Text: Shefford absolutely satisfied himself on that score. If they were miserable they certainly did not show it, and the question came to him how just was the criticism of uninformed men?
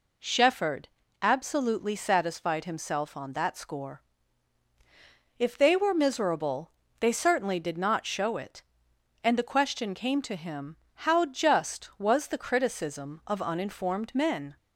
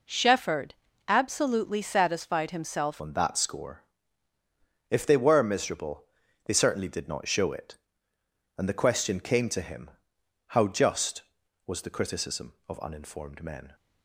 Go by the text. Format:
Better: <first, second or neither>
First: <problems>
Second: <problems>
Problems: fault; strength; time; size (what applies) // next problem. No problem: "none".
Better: first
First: pauses between "Shefford" and "absolutely"; slight; at 0.8 s; 0.32 s long // pauses between "miserable" and "they"; slight; at 6.7 s; 0.28 s long // pauses between "him" and "how"; slight; at 10.7 s; 0.32 s long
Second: pauses between "Shefford" and "absolutely"; slight; at 0.7 s; 0.32 s long // changes voice at "on"; from 2.9 s on; 10.8 s long // pauses between "miserable" and "they"; at 6.0 s; 0.42 s long // pauses between "him" and "how"; noticeable; at 9.9 s; 0.56 s long